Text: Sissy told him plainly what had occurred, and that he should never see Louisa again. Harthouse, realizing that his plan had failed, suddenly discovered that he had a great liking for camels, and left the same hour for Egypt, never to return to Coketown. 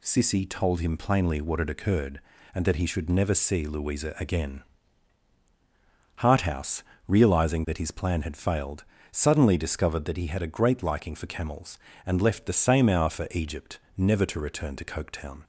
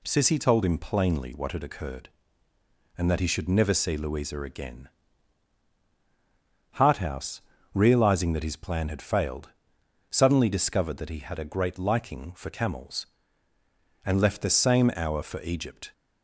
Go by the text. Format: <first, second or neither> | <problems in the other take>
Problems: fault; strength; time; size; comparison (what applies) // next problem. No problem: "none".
first | stops before "never to return to Coketown"; at 15.9 s